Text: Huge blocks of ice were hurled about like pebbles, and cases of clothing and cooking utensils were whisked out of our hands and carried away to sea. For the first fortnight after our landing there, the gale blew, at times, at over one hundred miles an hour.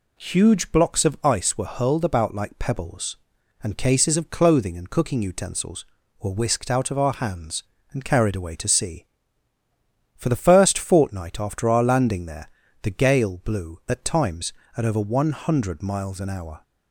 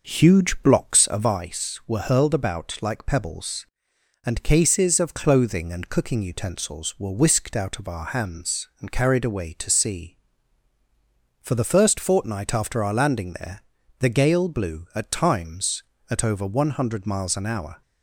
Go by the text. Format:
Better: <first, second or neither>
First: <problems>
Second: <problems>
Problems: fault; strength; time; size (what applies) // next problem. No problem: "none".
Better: first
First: none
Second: starts louder than the rest; noticeable; until 1.5 s; 6 dB